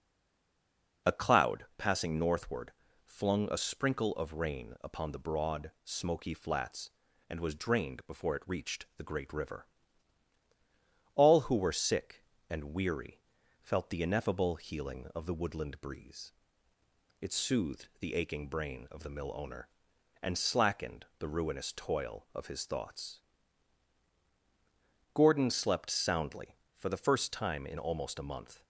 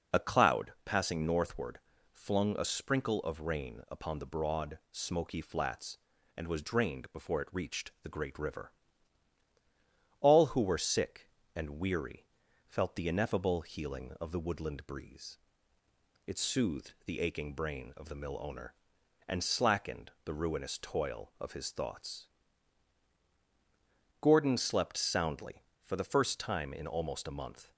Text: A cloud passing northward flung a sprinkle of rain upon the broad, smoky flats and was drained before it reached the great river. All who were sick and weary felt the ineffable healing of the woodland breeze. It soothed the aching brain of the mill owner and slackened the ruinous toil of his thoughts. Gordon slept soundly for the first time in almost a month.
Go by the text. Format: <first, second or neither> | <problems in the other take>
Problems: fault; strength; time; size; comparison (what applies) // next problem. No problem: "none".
second | stays silent before the first word; until 1.0 s; 1.0 s long // pauses between "northward" and "flung"; slight; at 2.7 s; 0.34 s long; slight in the second // pauses between "weary" and "felt"; at 13.2 s; 0.40 s long; also in the second